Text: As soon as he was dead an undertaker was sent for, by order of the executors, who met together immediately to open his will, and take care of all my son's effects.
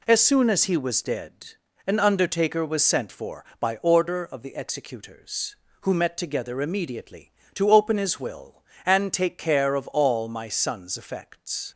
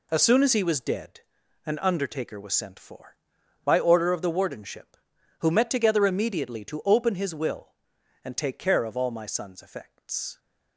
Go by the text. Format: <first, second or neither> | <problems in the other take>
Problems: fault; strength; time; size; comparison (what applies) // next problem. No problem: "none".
first | pauses between "dead" and "an"; noticeable; at 1.1 s; 0.46 s long; noticeable in the first // says "wardenship" for "executors"; at 4.3 s